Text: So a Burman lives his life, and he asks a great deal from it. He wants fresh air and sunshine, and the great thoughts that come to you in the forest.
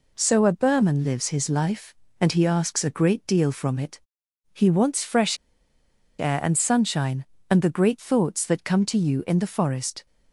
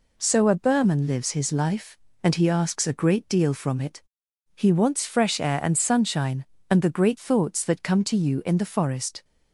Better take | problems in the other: second | pauses between "fresh" and "air"; noticeable; at 5.3 s; 0.84 s long

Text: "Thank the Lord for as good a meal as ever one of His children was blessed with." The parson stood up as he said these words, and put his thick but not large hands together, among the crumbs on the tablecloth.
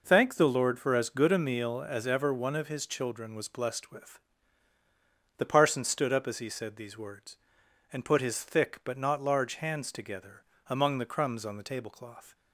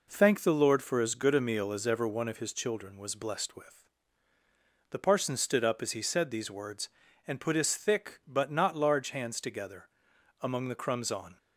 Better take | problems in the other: first | stops before "the tablecloth"; at 11.3 s

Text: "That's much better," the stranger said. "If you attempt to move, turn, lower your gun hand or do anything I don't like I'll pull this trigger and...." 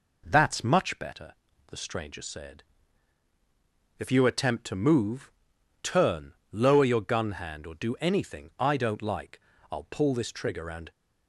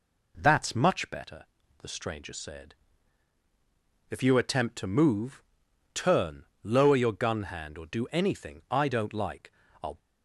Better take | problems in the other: first | pauses between "like" and "I'll"; slight; at 9.4 s; 0.32 s long; slight in the first // stops before "pull this trigger and"; at 9.9 s

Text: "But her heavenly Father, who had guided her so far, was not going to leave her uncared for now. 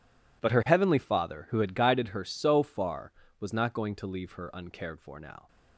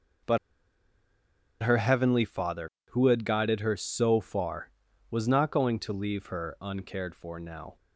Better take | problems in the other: first | pauses between "But" and "her"; strong; at 0.3 s; 1.2 s long

